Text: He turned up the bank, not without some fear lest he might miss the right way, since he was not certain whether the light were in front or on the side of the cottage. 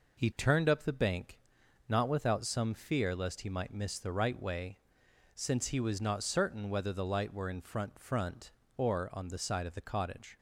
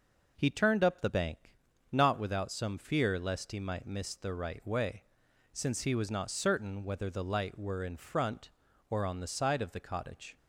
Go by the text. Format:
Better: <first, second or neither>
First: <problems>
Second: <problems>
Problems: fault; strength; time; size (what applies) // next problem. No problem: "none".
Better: second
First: says "front" twice; at 7.9 s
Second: none